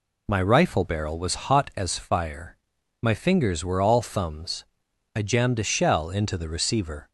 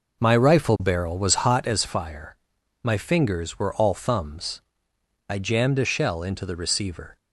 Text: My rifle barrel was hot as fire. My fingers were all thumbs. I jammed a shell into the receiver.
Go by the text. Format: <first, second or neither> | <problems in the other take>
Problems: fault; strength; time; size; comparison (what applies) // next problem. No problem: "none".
first | starts louder than the rest; noticeable; until 1.8 s; 5 dB